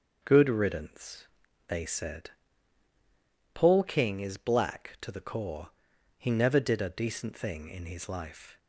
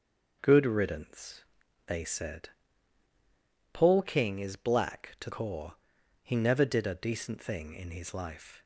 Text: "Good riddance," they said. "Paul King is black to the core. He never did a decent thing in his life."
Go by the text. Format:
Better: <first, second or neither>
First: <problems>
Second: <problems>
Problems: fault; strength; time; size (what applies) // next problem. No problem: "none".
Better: first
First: starts louder than the rest; until 1.2 s; 6.5 dB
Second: starts louder than the rest; noticeable; until 1.4 s; 6 dB // skips "the"; at 5.2 s